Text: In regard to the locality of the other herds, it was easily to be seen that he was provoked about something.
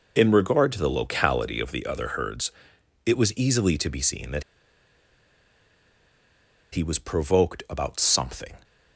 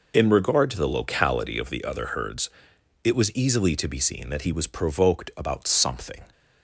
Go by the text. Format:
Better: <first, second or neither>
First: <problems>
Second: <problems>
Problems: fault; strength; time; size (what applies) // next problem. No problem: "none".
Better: second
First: pauses between "that" and "he"; strong; at 4.4 s; 2.3 s long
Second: none